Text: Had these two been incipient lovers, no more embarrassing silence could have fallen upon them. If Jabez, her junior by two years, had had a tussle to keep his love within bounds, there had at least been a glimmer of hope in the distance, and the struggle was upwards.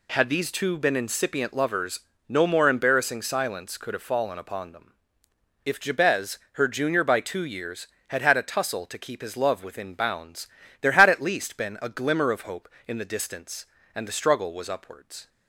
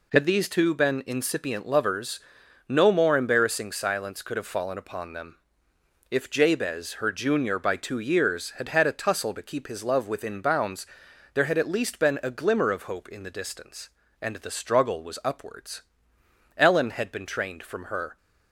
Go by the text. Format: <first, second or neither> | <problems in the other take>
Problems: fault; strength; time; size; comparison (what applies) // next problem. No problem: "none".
first | goes on to say "Ellen had been trained from her"; from 16.5 s on; 1.6 s long